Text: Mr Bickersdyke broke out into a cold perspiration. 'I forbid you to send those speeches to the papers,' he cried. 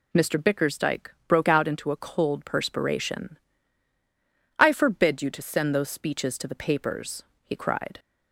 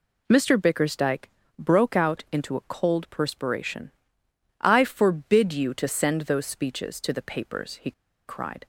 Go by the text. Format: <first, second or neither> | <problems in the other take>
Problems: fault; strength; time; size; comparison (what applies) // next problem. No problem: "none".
first | pauses between "Bickersdyke" and "broke"; slight; at 1.2 s; 0.34 s long; slight in the first // pauses between "he" and "cried"; at 7.9 s; 0.36 s long